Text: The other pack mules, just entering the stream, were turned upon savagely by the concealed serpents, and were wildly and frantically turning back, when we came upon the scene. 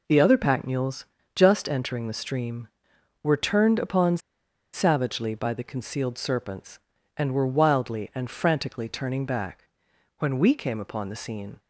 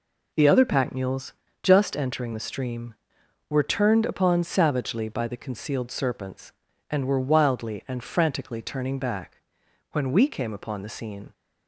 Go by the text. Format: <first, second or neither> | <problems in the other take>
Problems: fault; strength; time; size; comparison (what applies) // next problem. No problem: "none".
second | pauses between "upon" and "savagely"; noticeable; at 4.1 s; 0.54 s long